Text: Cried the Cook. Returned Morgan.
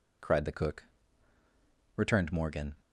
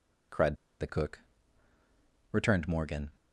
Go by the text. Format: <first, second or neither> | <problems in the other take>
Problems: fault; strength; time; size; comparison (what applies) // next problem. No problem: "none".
first | pauses between "Cried" and "the"; slight; at 0.5 s; 0.24 s long